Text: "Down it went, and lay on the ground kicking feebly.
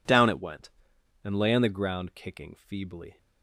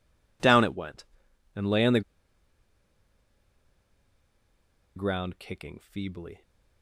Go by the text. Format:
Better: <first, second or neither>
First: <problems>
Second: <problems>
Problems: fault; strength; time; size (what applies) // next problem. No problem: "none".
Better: first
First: none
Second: pauses between "the" and "ground"; strong; at 2.0 s; 2.9 s long